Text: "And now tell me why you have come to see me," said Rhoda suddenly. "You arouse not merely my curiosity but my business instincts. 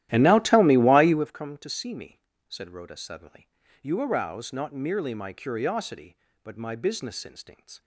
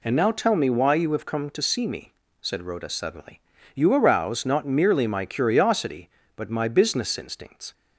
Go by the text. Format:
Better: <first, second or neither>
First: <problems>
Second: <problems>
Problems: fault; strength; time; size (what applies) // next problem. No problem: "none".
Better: second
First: starts louder than the rest; strong; until 1.3 s; 14 dB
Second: none